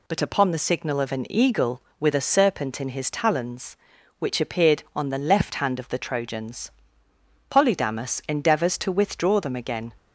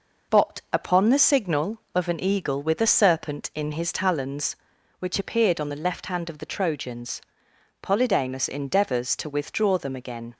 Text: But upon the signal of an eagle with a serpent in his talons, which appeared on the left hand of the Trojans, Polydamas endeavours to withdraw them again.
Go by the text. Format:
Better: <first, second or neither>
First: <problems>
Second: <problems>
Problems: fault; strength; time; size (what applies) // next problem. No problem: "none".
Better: neither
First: none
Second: none